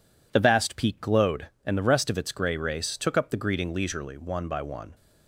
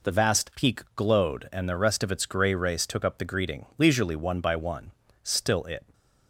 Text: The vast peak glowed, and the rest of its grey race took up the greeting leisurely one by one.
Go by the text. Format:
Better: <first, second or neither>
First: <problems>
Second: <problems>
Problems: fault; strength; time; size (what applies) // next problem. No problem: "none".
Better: first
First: none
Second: pauses between "peak" and "glowed"; slight; at 0.8 s; 0.16 s long // goes on to say "Still it"; noticeable; from 5.2 s on; 0.70 s long